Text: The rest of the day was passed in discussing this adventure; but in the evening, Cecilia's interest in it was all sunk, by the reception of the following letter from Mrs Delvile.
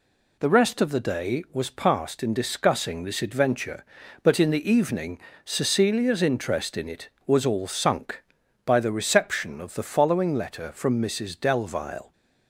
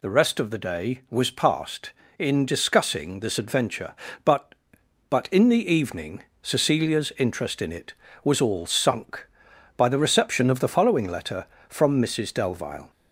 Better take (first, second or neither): first